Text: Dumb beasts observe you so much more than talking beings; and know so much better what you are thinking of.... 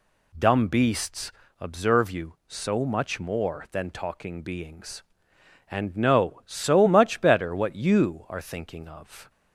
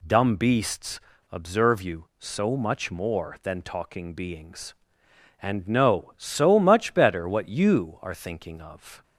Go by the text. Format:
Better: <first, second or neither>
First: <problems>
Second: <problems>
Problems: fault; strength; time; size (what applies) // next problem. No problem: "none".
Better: neither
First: pauses between "beasts" and "observe"; slight; at 1.3 s; 0.28 s long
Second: pauses between "beasts" and "observe"; slight; at 0.9 s; 0.31 s long